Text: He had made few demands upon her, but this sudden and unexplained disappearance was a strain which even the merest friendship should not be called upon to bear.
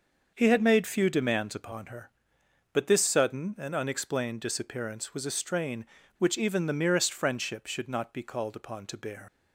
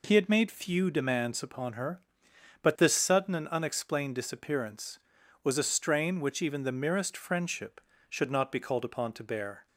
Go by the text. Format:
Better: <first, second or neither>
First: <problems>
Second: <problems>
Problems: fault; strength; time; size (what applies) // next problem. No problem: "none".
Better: second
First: starts louder than the rest; until 1.3 s; 6 dB // leaves "bear" unfinished; at 9.2 s; 110 ms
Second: none